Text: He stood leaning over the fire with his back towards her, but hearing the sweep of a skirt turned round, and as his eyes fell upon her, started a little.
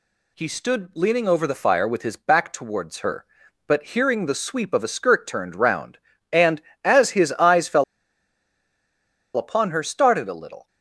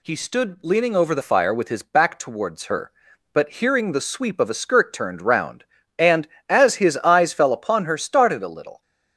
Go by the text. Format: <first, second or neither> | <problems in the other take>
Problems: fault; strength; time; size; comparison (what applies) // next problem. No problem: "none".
second | pauses between "fell" and "upon"; strong; at 7.8 s; 1.5 s long